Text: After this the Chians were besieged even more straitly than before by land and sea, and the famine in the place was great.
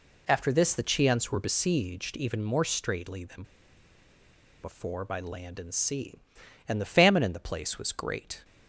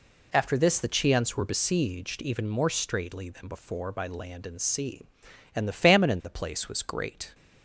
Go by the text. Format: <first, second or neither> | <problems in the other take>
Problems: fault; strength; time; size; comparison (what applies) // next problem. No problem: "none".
second | pauses between "than" and "before"; at 3.4 s; 1.1 s long